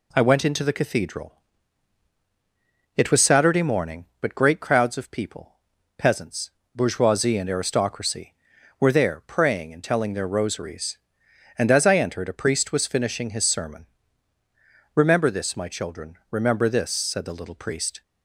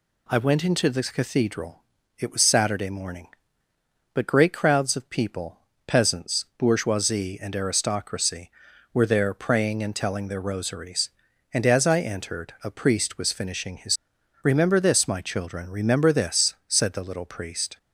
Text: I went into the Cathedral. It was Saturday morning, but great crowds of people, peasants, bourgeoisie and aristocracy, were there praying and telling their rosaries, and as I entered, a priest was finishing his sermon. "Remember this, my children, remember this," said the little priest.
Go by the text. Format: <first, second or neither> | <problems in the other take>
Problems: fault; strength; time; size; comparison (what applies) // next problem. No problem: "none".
first | skips "sermon"; at 14.1 s